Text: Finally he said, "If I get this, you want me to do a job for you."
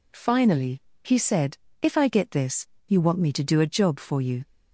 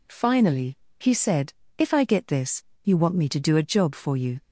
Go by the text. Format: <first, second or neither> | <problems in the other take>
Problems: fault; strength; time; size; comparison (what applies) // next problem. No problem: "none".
neither | pauses between "Finally" and "he"; slight; the same in both